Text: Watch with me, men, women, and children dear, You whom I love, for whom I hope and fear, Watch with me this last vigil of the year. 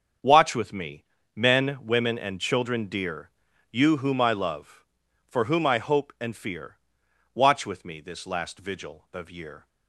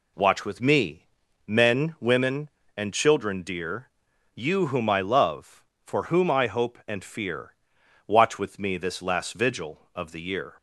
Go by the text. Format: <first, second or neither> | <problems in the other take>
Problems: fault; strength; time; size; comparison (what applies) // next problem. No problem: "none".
second | starts louder than the rest; strong; until 1.5 s; 7.5 dB // skips "the"; at 9.3 s